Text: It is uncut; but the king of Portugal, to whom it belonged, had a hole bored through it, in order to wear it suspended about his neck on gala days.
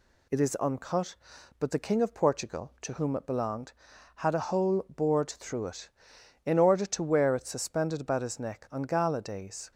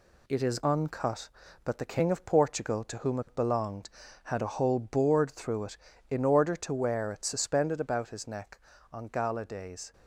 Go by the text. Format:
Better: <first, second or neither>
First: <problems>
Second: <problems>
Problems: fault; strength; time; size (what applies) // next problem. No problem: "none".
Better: first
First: none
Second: gets quieter; noticeable; throughout; 5 dB